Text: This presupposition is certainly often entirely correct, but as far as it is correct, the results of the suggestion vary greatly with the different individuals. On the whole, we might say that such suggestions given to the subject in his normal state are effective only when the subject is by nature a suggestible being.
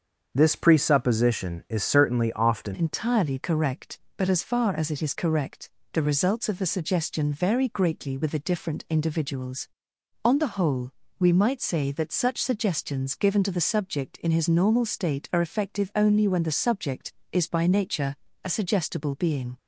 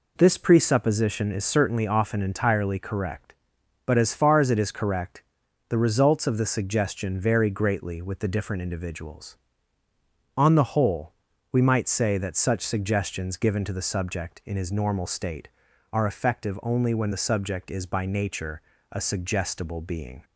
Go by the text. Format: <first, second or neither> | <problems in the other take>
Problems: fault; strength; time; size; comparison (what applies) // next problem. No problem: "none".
second | starts louder than the rest; until 1.3 s; 7 dB // changes voice at "entirely"; from 2.7 s on; 16.8 s long // pauses between "nature" and "a"; slight; at 18.1 s; 0.30 s long; slight in the second